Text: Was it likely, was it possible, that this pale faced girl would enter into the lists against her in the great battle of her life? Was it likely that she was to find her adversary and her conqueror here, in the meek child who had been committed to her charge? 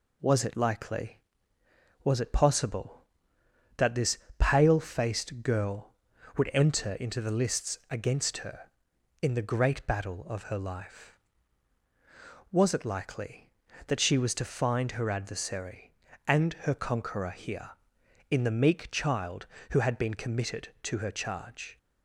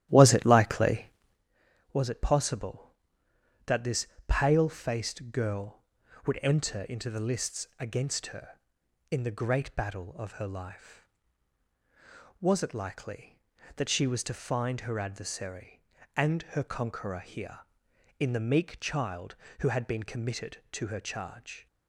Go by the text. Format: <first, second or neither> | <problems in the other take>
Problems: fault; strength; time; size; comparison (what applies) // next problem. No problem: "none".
first | starts louder than the rest; strong; until 1.4 s; 13.5 dB // pauses between "this" and "pale"; slight; at 4.0 s; 0.20 s long; slight in the first